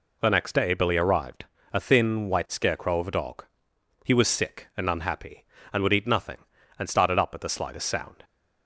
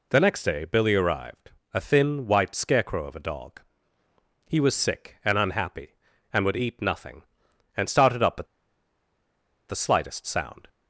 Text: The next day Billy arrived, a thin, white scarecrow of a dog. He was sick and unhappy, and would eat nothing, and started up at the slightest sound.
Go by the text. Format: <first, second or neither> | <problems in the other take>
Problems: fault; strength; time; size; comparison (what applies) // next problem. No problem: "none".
first | pauses between "at" and "the"; at 8.4 s; 1.2 s long